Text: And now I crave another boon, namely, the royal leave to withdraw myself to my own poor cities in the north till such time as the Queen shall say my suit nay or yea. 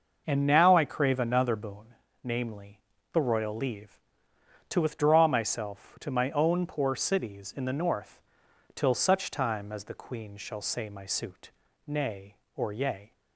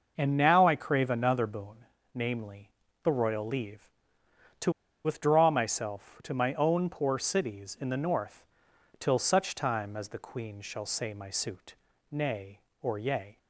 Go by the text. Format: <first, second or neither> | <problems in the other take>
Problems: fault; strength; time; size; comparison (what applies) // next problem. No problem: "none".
first | pauses between "to" and "withdraw"; slight; at 4.7 s; 0.33 s long // pauses between "north" and "till"; noticeable; at 8.4 s; 0.52 s long; noticeable in the first // pauses between "suit" and "nay"; slight; at 11.7 s; 0.34 s long; slight in the first